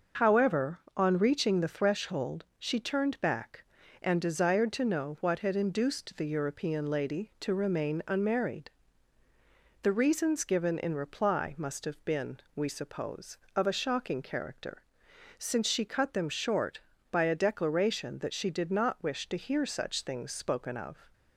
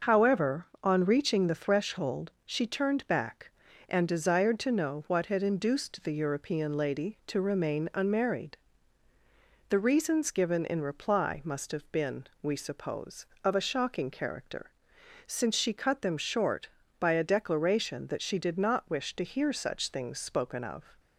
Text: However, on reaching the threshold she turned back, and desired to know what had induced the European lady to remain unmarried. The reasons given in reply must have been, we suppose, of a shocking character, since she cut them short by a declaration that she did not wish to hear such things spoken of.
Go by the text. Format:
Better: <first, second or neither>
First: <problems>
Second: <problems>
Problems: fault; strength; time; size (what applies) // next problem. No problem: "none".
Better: neither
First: starts louder than the rest; until 1.3 s; 6.5 dB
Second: starts louder than the rest; noticeable; until 1.2 s; 6 dB